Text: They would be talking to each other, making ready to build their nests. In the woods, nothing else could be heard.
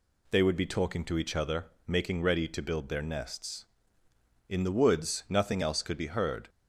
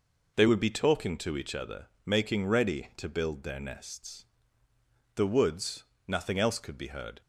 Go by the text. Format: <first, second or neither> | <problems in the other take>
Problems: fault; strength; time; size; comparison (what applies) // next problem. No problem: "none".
first | skips "In"; at 4.7 s